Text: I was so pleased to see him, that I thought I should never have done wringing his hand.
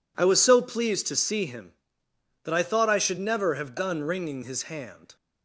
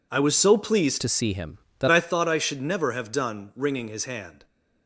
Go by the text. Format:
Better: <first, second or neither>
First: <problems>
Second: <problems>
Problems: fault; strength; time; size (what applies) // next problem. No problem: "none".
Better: first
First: none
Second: changes voice from "to" to "that"; from 1.0 to 1.8 s; 0.8 s long